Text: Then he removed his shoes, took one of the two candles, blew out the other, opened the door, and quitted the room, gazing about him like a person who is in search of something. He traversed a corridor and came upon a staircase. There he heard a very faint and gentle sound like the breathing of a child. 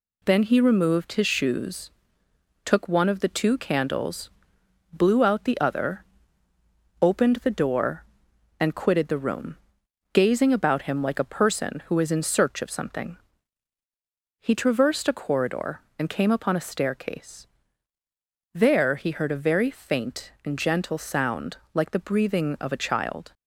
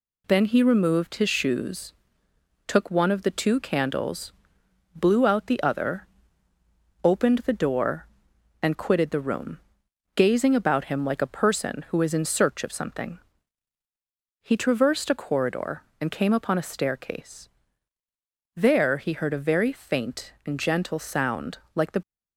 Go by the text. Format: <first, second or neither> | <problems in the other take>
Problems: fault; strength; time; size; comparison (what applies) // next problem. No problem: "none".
first | pauses between "sound" and "like"; slight; at 21.5 s; 0.16 s long; slight in the first // stops before "breathing of a child"; at 22.0 s